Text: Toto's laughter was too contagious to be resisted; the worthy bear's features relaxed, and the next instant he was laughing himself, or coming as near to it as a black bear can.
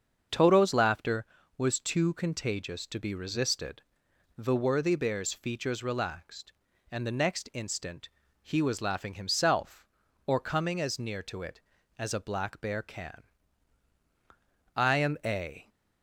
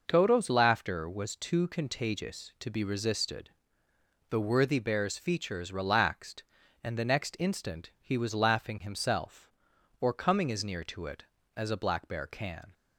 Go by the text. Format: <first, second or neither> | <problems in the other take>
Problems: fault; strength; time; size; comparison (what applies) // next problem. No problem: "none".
second | starts louder than the rest; until 1.6 s; 6.5 dB // pauses between "instant" and "he"; slight; at 8.0 s; 0.34 s long // goes on to say "I am a"; noticeable; from 14.7 s on; 0.94 s long